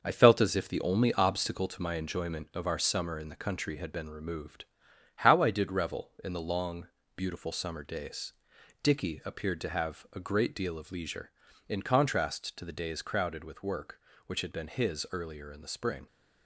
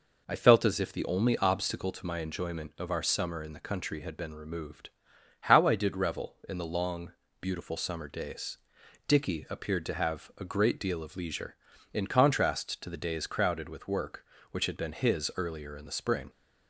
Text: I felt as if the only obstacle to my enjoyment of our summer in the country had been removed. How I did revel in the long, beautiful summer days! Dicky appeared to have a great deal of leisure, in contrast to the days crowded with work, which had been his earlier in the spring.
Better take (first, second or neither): second